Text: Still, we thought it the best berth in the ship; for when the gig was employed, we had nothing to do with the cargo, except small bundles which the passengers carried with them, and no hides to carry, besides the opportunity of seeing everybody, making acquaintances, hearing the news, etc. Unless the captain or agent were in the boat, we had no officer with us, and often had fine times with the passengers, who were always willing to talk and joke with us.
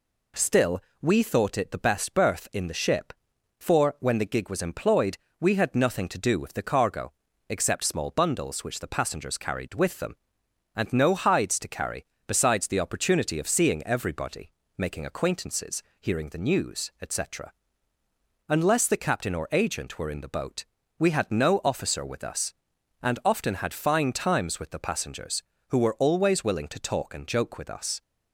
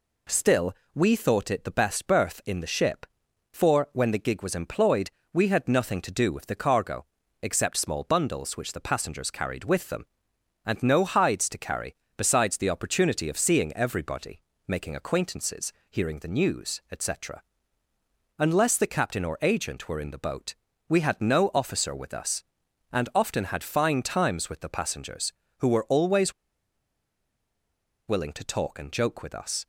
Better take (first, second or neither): first